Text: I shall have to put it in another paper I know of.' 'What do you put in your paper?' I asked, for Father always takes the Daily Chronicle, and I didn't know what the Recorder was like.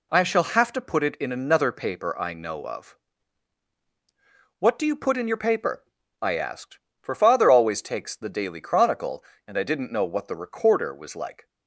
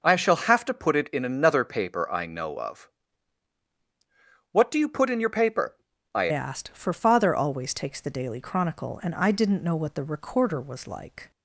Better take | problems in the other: first | changes voice at "asked"; from 6.3 s on; 5.0 s long

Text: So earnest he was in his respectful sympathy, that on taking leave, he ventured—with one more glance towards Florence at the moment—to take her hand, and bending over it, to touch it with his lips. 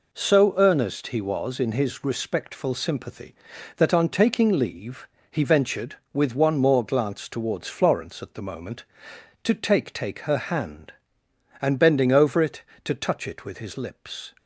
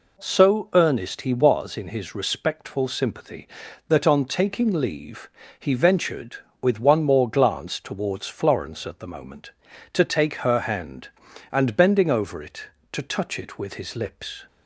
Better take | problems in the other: second | says "take" twice; at 9.9 s

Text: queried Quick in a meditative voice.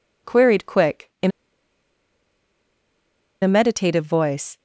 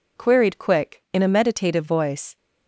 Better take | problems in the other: second | pauses between "in" and "a"; strong; at 1.3 s; 2.1 s long

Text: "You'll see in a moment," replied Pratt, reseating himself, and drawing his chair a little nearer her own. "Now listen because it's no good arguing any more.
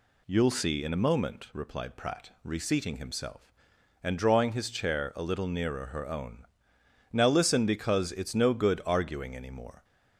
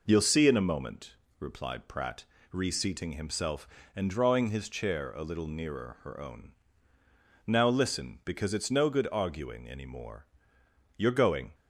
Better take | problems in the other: first | goes on to say "You're going"; from 10.9 s on; 0.58 s long

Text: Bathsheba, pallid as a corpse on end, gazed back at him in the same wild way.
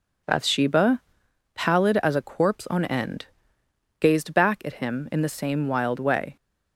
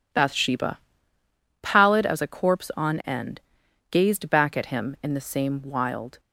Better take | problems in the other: first | stops before "way"; at 6.1 s

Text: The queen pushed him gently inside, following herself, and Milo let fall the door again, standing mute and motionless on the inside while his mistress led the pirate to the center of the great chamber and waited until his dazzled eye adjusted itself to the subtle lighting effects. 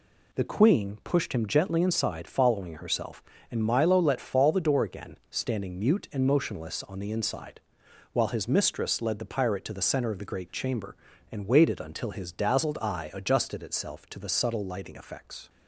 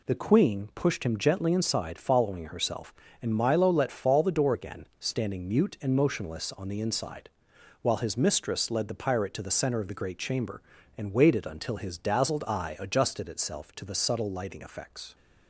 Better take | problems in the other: neither | pauses between "inside" and "while"; noticeable; the same in both

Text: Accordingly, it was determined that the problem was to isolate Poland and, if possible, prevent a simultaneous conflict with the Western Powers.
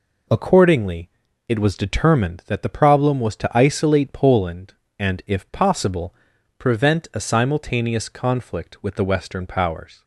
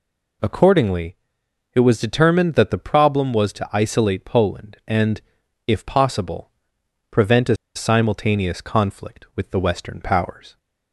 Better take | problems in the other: first | pauses between "a" and "simultaneous"; slight; at 7.5 s; 0.19 s long

